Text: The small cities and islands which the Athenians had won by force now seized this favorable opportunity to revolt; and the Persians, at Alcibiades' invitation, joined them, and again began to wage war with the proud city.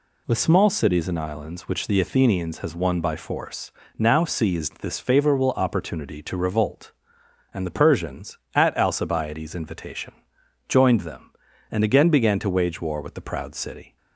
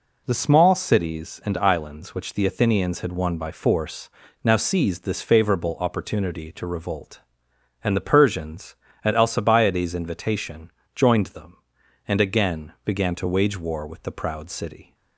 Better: second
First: says "has" for "had"; at 2.5 s // pauses between "force" and "now"; slight; at 3.7 s; 0.28 s long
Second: pauses between "force" and "now"; slight; at 4.0 s; 0.36 s long

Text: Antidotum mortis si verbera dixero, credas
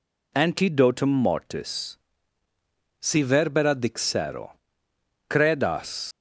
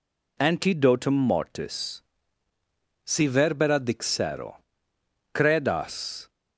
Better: second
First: pauses between "mortis" and "si"; at 1.9 s; 1.0 s long // leaves "credas" unfinished; at 6.1 s; 135 ms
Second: pauses between "mortis" and "si"; at 2.0 s; 1.0 s long

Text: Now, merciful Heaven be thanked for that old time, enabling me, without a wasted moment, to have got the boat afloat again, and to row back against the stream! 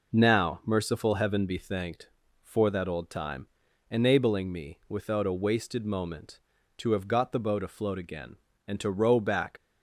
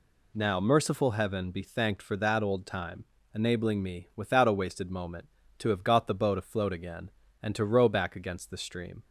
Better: second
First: stops before "against the stream"; at 9.5 s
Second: none

